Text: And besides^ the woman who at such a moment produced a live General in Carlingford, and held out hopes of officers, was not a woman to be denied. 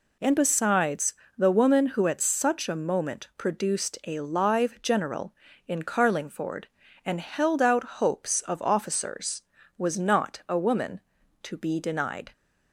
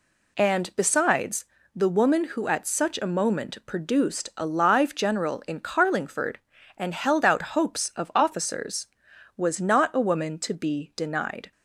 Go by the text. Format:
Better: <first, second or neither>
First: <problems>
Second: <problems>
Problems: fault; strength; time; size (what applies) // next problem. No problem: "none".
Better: neither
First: pauses between "besides" and "the"; slight; at 1.1 s; 0.24 s long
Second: pauses between "besides" and "the"; slight; at 1.4 s; 0.30 s long